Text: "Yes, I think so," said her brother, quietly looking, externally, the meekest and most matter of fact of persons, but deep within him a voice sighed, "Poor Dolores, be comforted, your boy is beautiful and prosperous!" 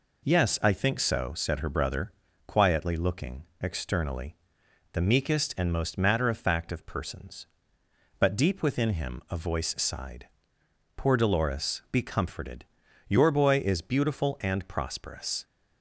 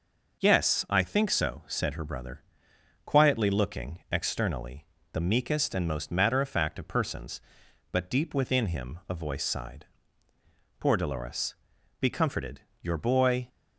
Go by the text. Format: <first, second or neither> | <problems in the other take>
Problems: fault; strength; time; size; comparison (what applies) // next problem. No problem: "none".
first | stops before "is beautiful and prosperous"; at 13.4 s